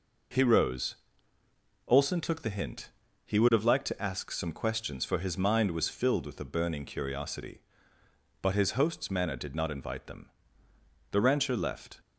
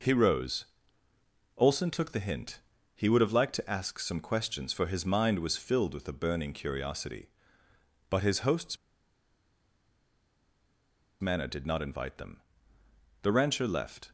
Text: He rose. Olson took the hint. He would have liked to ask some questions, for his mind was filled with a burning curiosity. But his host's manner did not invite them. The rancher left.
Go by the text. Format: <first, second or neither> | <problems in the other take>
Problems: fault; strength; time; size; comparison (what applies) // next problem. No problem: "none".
first | pauses between "host's" and "manner"; strong; at 8.7 s; 2.4 s long